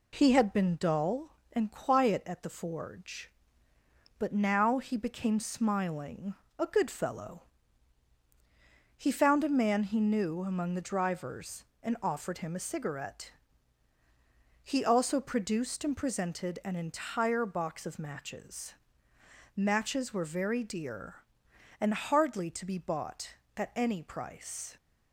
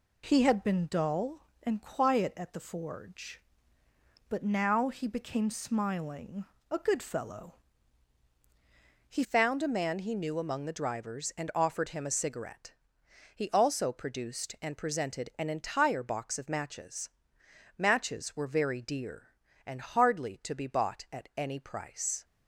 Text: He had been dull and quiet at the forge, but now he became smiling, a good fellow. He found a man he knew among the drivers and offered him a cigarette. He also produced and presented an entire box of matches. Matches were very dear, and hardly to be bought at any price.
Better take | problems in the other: first | changes voice at "found"; from 9.2 s on; 13.0 s long

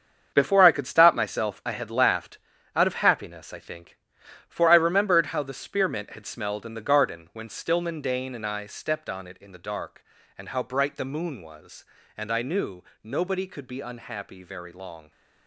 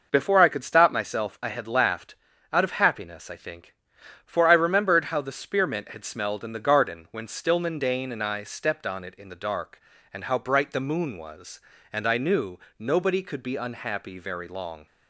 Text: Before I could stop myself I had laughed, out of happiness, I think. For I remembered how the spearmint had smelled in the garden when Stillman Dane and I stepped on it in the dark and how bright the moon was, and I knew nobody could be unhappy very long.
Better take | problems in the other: second | gets quieter; strong; throughout; 9 dB // pauses between "knew" and "nobody"; slight; at 12.8 s; 0.22 s long; slight in the second

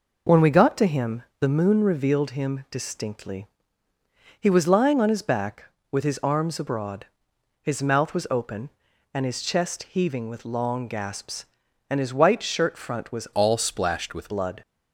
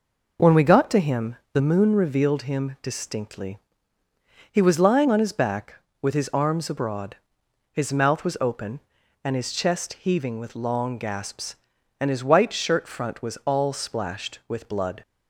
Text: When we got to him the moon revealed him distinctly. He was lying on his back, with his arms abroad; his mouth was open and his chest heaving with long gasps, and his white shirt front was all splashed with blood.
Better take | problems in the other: second | pauses between "him" and "the"; slight; at 1.2 s; 0.18 s long; slight in the second // changes voice from "all" to "with"; from 13.3 to 14.2 s; 0.9 s long

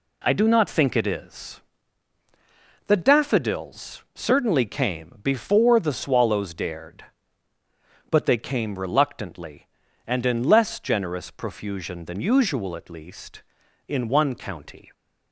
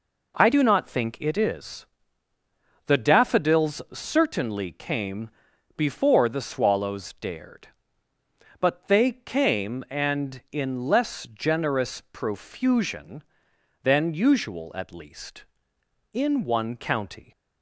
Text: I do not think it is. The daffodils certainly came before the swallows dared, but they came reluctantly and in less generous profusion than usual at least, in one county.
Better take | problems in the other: first | pauses between "came" and "before"; noticeable; at 5.2 s; 0.48 s long // skips "reluctantly"; at 9.8 s

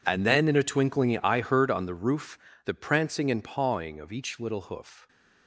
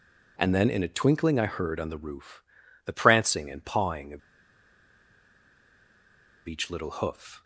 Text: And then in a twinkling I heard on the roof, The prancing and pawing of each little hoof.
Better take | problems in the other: first | pauses between "of" and "each"; strong; at 4.1 s; 2.2 s long

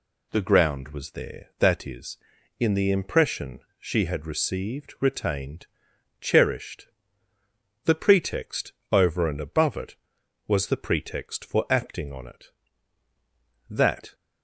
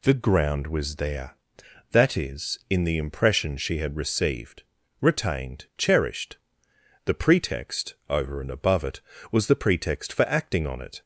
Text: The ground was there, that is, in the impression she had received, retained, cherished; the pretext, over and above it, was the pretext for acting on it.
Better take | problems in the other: second | pauses between "impression" and "she"; slight; at 3.6 s; 0.18 s long // goes on to say "That"; slight; from 13.7 s on; 0.44 s long

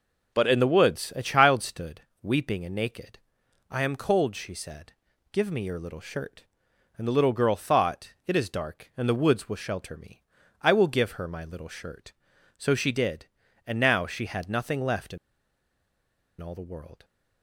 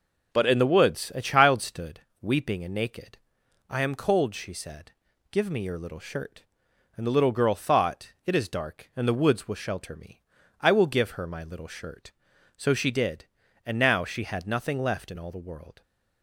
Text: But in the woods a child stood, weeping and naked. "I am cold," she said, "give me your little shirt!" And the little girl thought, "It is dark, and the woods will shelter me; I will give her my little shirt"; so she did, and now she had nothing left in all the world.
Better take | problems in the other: second | pauses between "in" and "all"; at 15.1 s; 1.2 s long

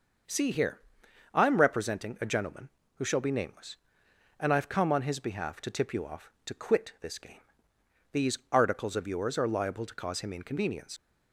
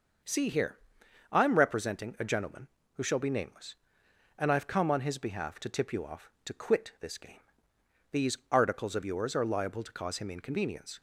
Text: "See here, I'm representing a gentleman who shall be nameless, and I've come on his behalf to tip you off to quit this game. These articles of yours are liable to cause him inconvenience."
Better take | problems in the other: second | leaves "inconvenience" unfinished; at 10.9 s; 60 ms

